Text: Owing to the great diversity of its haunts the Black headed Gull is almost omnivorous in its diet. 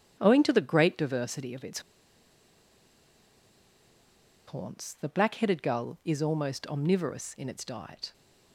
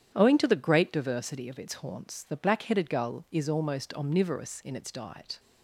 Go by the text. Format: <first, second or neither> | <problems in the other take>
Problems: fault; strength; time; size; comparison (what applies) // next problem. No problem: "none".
second | starts louder than the rest; strong; until 1.2 s; 10 dB; strong in the second // pauses between "its" and "haunts"; strong; at 1.7 s; 2.6 s long